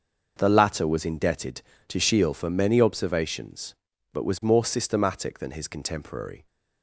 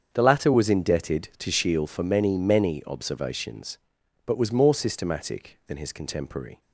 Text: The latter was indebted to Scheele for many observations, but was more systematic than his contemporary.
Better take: first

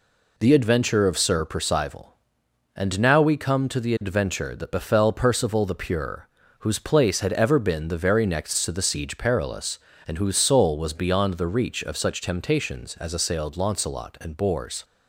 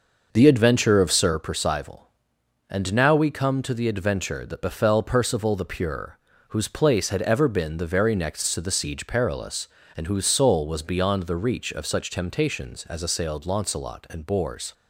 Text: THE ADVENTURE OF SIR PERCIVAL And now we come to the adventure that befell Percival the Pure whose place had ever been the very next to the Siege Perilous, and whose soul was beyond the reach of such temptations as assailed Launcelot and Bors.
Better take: first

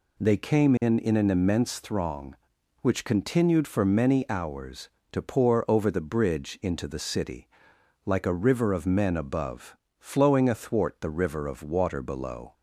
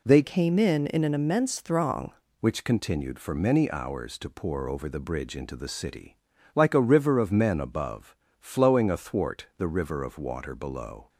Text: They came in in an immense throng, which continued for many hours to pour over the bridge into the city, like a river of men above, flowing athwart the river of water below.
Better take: first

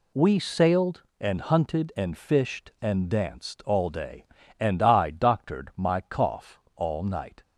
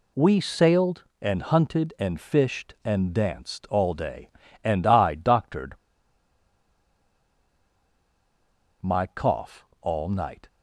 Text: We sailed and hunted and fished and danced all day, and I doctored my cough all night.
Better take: first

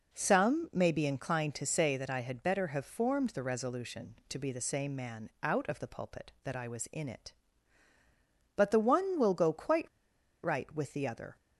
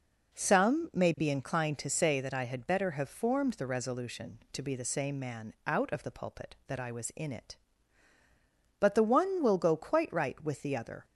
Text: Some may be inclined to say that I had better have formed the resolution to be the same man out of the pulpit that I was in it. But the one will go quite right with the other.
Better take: second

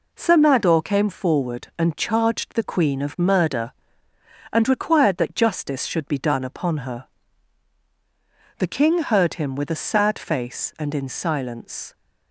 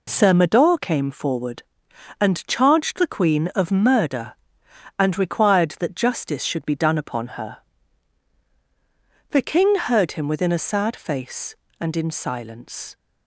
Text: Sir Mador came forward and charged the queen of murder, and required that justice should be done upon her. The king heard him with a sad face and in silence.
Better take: first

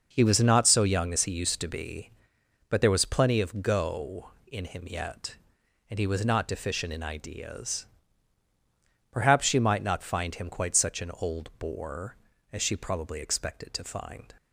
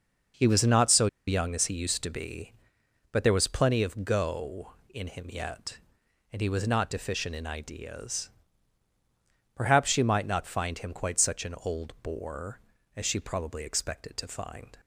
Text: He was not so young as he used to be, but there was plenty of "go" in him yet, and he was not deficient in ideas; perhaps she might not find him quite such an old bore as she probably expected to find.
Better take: first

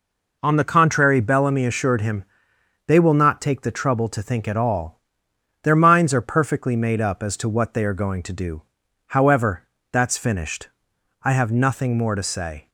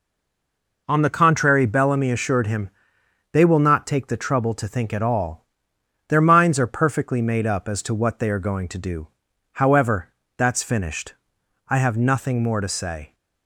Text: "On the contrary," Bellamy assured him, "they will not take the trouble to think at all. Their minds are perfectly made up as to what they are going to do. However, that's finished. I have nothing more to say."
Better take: first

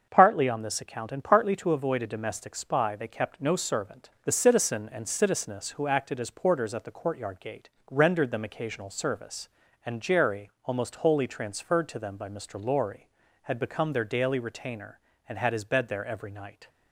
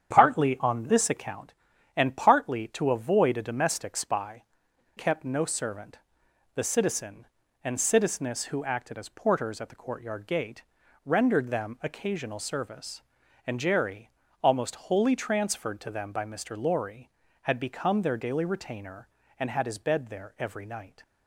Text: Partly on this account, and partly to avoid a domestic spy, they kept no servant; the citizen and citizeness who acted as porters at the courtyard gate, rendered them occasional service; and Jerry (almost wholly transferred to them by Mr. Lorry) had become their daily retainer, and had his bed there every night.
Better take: first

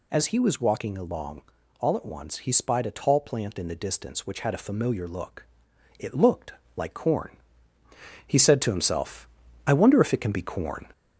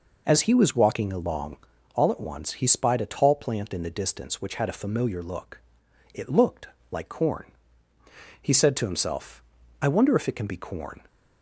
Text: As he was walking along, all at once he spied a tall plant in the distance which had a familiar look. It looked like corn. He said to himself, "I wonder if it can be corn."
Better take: second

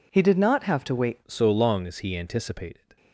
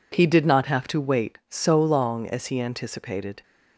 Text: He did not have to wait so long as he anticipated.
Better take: second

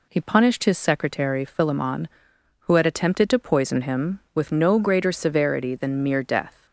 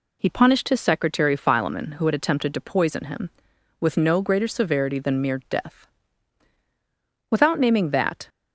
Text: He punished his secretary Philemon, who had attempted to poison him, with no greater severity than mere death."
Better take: first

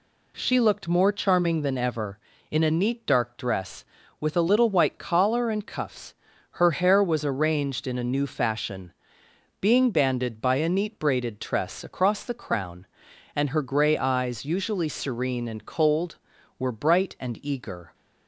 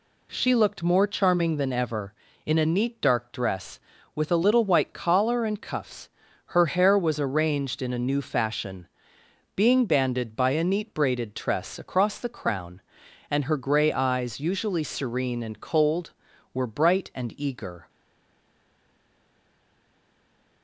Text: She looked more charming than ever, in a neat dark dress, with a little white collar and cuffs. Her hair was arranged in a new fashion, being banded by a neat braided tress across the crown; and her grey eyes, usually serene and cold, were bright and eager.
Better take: first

